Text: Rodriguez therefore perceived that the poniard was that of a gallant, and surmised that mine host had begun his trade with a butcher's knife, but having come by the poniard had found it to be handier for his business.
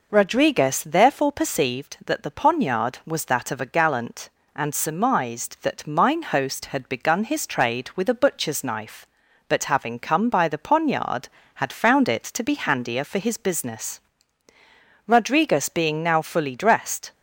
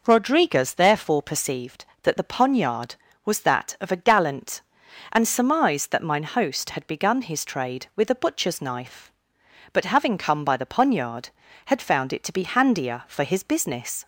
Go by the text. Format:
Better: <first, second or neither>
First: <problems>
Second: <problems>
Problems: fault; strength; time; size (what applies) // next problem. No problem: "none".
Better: second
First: goes on to say "Rodriguez being now fully dressed"; strong; from 15.0 s on; 2.0 s long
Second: none